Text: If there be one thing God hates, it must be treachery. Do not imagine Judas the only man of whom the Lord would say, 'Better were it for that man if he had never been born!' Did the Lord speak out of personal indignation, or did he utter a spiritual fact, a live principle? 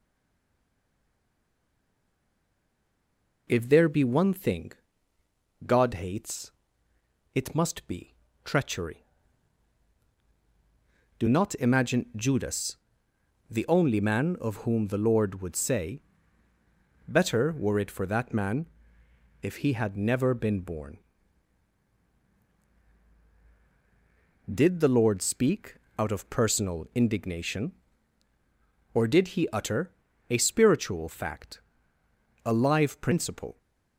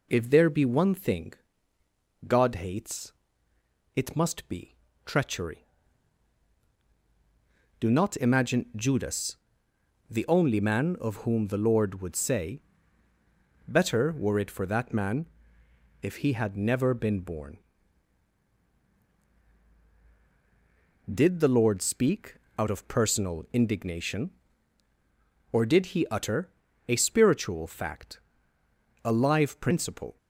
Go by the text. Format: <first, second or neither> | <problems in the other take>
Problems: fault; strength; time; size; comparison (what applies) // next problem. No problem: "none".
second | stays silent before the first word; strong; until 3.4 s; 3.4 s long // pauses between "thing" and "God"; noticeable; at 4.7 s; 0.94 s long; noticeable in the second // pauses between "be" and "treachery"; slight; at 8.1 s; 0.32 s long; slight in the second // pauses between "Judas" and "the"; noticeable; at 12.7 s; 0.74 s long; noticeable in the second // pauses between "man" and "if"; noticeable; at 18.6 s; 0.78 s long; noticeable in the second // pauses between "speak" and "out"; slight; at 25.7 s; 0.22 s long; slight in the second // pauses between "utter" and "a"; at 29.9 s; 0.40 s long; also in the second